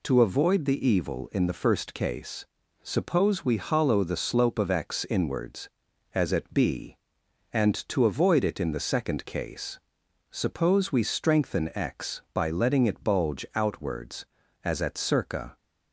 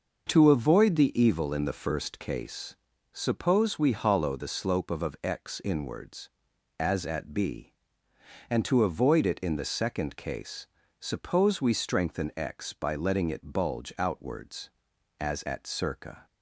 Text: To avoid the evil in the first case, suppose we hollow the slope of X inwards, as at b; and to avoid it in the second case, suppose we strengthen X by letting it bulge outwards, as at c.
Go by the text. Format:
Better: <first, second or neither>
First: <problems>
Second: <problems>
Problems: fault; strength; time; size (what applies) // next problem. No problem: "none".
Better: first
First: none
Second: says "of" twice; at 5.0 s